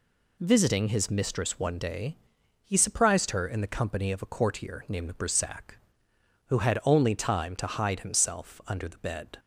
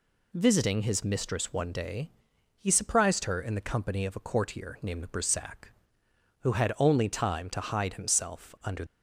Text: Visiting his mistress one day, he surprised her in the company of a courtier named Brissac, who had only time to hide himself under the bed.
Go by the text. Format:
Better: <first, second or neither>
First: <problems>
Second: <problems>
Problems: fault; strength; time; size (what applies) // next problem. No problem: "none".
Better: first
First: none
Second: stops before "the bed"; at 8.8 s